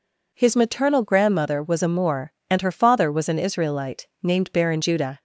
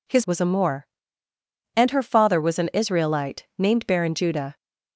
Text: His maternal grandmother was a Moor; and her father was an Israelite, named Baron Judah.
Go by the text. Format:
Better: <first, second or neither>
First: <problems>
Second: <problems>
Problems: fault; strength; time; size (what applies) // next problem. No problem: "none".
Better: first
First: none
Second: skips "maternal grandmother"; at 0.2 s